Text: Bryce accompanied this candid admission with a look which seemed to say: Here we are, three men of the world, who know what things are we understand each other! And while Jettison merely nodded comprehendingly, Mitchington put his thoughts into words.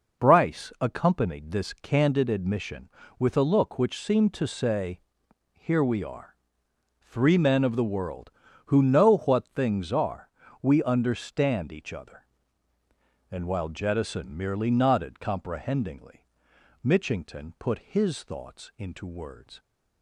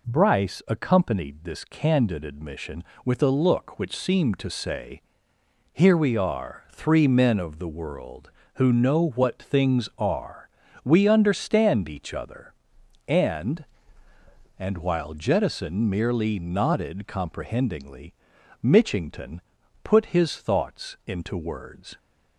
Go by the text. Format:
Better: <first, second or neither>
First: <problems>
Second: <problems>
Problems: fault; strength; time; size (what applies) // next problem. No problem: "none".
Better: first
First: pauses between "are" and "we"; slight; at 10.2 s; 0.32 s long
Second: pauses between "are" and "we"; at 10.4 s; 0.40 s long // says "And" twice; at 14.5 s // pauses between "Mitchington" and "put"; at 19.4 s; 0.42 s long